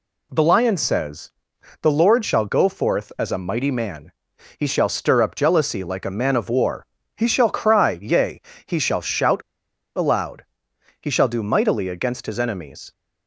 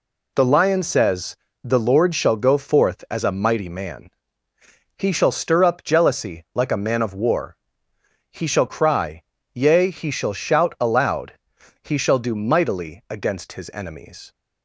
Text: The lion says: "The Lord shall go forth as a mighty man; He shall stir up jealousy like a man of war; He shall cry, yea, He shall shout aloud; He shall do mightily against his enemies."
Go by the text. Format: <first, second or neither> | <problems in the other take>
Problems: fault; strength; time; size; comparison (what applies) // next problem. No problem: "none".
second | pauses between "shout" and "aloud"; noticeable; at 9.4 s; 0.55 s long